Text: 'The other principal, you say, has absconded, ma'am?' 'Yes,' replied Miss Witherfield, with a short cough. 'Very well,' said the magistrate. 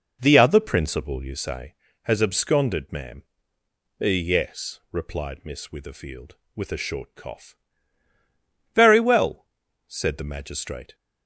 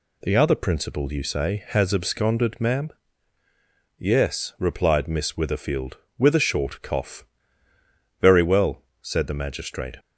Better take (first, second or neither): second